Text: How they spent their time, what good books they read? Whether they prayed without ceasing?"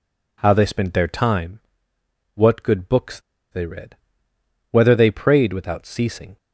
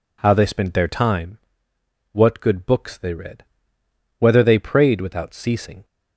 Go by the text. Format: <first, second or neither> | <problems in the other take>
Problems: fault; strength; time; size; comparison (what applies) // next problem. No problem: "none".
second | pauses between "books" and "they"; slight; at 3.1 s; 0.32 s long